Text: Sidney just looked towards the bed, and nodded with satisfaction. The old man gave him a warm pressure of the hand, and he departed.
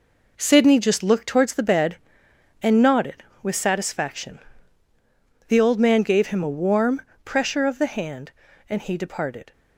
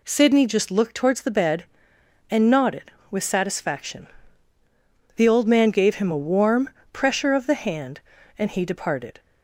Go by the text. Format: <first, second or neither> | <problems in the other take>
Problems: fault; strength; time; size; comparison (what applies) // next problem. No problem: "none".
second | gets quieter; strong; throughout; 9 dB // pauses between "warm" and "pressure"; slight; at 7.0 s; 0.20 s long; slight in the second